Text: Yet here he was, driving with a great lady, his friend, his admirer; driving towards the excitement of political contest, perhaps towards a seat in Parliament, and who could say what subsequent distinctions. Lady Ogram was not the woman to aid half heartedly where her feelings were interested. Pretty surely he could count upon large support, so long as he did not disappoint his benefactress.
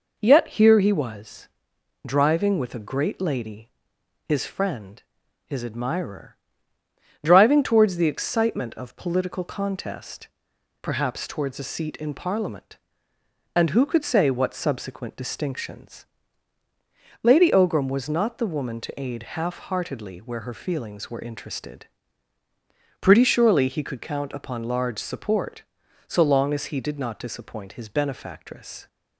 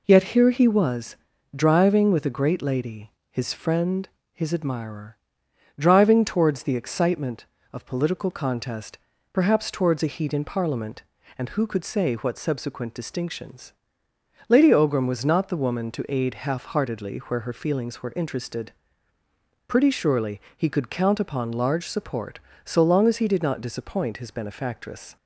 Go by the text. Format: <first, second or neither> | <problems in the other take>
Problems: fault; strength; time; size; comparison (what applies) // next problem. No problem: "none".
first | says "heat" for "seat"; at 10.1 s // pauses between "surely" and "he"; slight; at 20.3 s; 0.16 s long